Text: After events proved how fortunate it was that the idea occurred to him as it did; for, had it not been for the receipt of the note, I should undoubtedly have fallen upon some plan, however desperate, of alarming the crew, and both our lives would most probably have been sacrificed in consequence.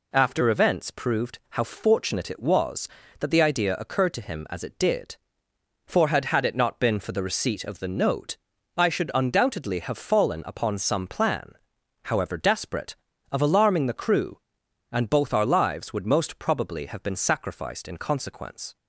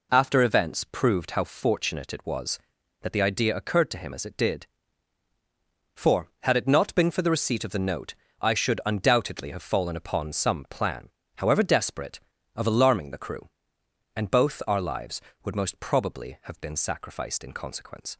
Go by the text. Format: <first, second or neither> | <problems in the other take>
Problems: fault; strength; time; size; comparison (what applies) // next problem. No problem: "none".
second | says "had" twice; at 6.2 s